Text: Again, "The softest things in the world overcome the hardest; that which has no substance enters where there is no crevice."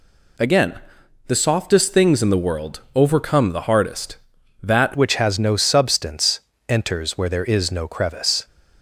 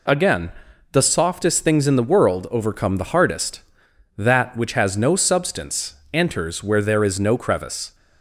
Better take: second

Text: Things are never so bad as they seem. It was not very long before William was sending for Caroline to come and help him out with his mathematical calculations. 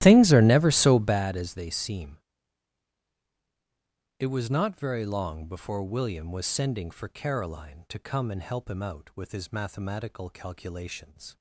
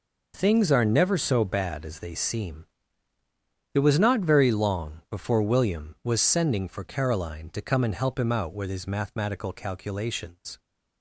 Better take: second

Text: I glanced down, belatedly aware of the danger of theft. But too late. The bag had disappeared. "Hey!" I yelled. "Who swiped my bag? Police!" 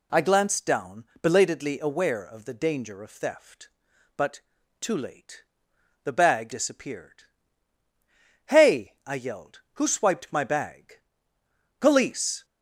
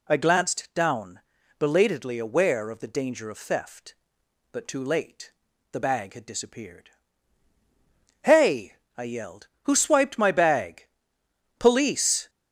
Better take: second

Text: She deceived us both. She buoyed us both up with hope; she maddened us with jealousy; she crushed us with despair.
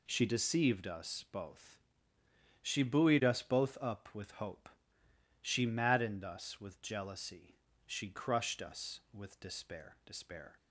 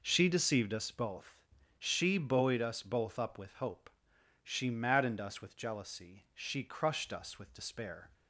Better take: second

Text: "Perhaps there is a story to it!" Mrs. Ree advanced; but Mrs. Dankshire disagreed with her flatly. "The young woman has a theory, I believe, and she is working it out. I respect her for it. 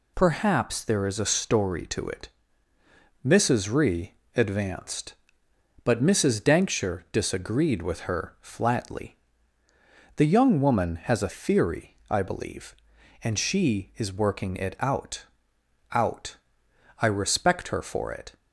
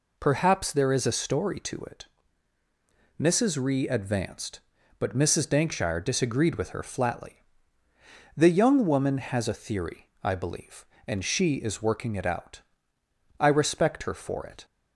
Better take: second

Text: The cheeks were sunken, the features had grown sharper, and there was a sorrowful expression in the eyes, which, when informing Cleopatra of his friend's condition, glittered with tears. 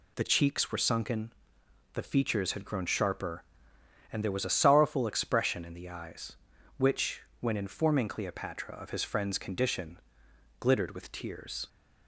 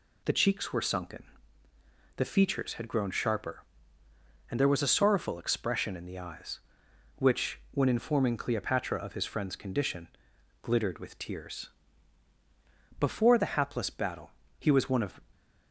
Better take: first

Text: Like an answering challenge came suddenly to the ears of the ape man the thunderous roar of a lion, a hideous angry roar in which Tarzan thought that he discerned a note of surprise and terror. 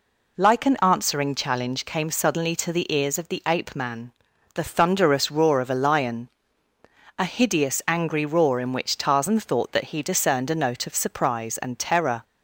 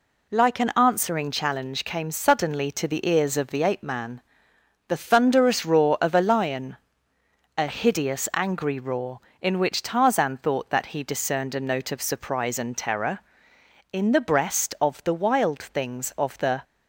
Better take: first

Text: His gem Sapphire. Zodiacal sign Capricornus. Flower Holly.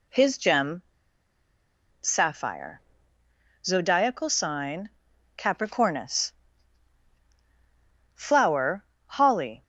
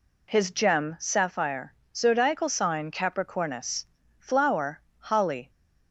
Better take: second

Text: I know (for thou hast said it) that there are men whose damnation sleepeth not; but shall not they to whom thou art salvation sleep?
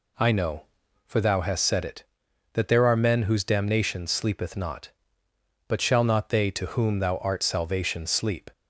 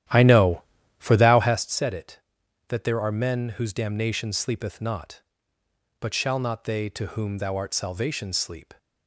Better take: first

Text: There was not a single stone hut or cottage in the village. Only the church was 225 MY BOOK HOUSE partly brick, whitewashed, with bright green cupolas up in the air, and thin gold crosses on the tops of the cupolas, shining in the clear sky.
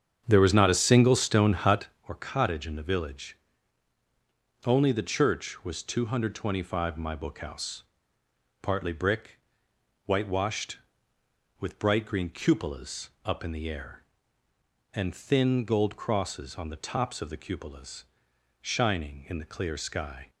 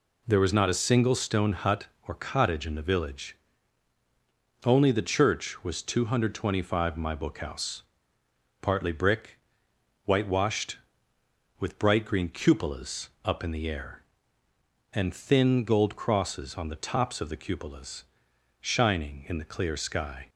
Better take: second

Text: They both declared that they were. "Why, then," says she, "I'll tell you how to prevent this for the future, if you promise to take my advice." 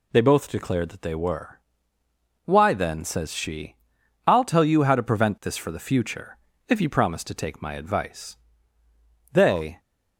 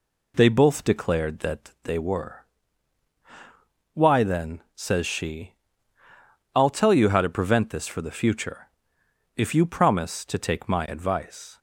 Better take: second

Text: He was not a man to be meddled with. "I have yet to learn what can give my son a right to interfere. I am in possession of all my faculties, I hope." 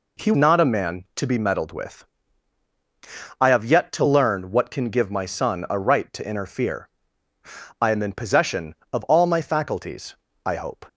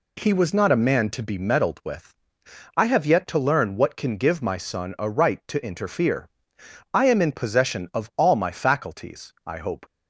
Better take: second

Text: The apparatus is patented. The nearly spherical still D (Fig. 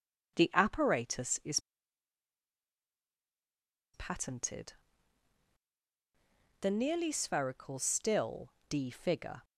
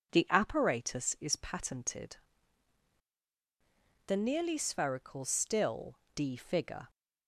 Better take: second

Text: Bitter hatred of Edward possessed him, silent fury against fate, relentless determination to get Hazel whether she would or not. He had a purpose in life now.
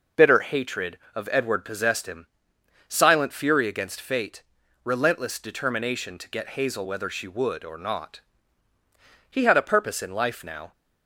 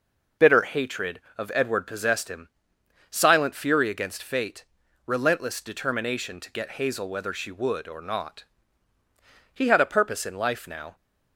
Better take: neither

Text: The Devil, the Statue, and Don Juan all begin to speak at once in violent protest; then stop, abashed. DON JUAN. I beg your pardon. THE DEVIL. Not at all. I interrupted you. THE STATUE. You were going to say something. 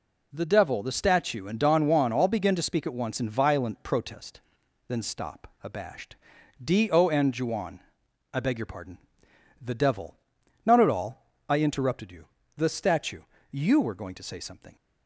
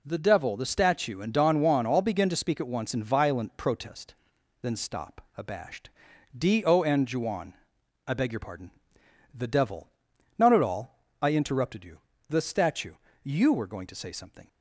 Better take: neither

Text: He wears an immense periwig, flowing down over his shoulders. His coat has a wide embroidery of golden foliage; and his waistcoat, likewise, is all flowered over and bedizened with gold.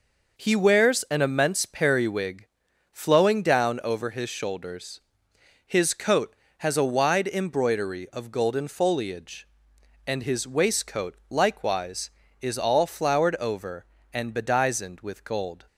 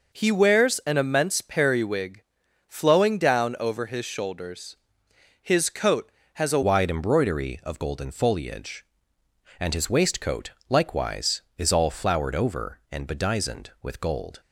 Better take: first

